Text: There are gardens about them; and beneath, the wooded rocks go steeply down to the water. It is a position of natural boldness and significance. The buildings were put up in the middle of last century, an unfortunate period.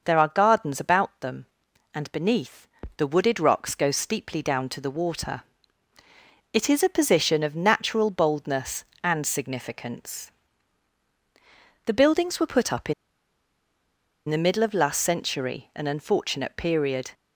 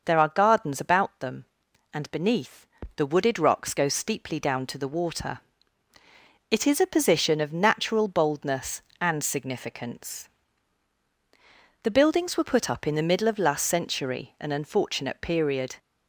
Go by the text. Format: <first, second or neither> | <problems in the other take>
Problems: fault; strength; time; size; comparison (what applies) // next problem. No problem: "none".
second | starts louder than the rest; noticeable; until 1.0 s; 6 dB; also in the second // pauses between "in" and "the"; strong; at 12.9 s; 1.3 s long